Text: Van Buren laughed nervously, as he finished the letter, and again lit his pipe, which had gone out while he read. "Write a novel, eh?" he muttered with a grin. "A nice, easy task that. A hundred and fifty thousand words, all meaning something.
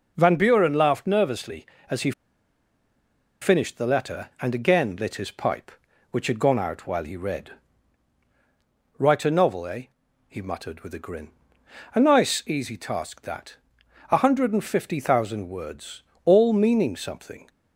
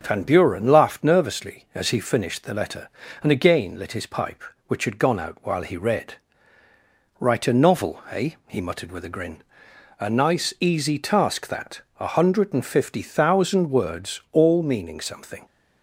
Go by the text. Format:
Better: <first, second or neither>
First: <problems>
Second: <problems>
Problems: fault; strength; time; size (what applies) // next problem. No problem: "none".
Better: second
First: pauses between "he" and "finished"; strong; at 2.1 s; 1.3 s long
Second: none